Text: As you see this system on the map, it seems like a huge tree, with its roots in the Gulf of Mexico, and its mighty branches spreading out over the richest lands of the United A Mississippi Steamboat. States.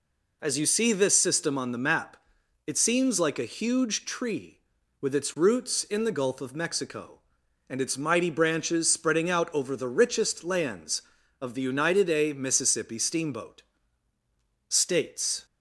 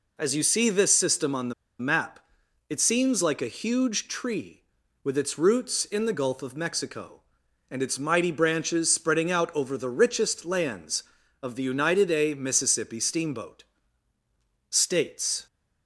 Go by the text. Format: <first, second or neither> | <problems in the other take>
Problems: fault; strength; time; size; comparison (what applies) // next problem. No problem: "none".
first | pauses between "the" and "map"; slight; at 1.5 s; 0.26 s long